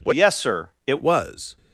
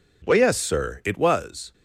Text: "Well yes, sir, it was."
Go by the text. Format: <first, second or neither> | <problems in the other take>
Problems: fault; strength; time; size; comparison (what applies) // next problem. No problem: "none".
second | changes voice from "yes" to "it"; from 0.1 to 1.0 s; 0.9 s long